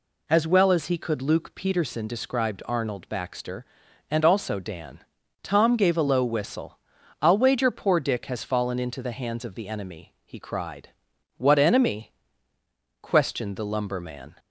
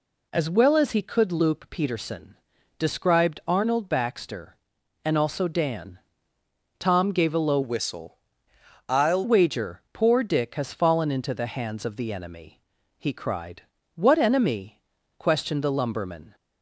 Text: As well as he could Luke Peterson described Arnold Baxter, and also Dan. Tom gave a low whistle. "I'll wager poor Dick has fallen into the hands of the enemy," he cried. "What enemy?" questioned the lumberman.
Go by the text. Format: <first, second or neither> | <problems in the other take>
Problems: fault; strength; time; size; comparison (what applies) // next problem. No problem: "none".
first | pauses between "Peterson" and "described"; at 2.3 s; 0.42 s long // changes voice from "whistle" to "I'll"; from 7.6 to 9.2 s; 1.6 s long